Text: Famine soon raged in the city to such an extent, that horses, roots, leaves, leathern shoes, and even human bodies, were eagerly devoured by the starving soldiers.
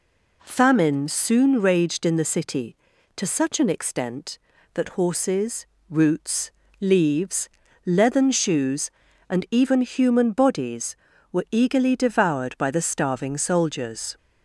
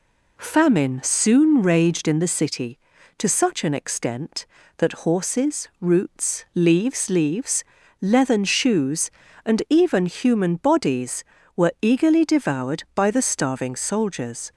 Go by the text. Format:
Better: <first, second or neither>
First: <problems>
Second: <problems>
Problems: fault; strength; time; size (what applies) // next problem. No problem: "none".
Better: first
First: none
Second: says "leaves" twice; at 7.0 s